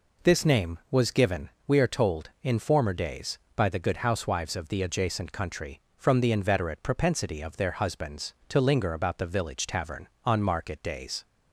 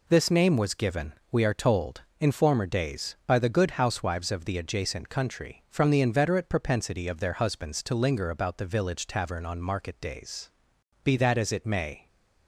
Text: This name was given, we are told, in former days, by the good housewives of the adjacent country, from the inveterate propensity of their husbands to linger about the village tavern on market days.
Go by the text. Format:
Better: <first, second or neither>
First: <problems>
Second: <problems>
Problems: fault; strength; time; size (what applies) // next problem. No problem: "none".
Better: first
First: none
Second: goes on to say "Be that as it may"; noticeable; from 11.0 s on; 1.0 s long